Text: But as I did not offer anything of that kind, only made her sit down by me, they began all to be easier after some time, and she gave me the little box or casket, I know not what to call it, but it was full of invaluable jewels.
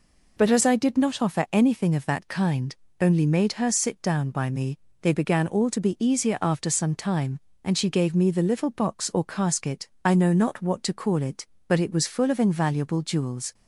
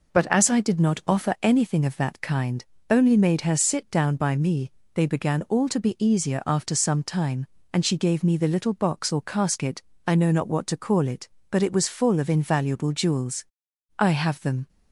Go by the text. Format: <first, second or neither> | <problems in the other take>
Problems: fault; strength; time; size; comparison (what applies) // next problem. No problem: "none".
first | goes on to say "I have them"; noticeable; from 13.9 s on; 0.70 s long